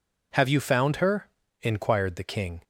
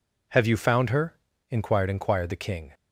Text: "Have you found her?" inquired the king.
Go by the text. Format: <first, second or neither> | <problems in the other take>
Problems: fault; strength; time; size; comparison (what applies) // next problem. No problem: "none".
first | says "inquired" twice; at 1.8 s